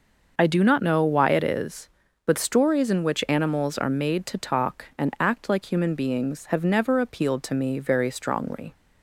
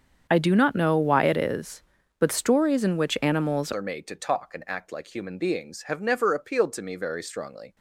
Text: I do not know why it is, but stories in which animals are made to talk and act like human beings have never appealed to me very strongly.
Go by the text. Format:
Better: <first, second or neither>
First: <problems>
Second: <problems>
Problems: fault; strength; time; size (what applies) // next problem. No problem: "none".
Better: first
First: starts louder than the rest; noticeable; until 1.4 s; 6 dB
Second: starts louder than the rest; strong; until 1.3 s; 7.5 dB // changes voice at "are"; from 3.7 s on; 4.0 s long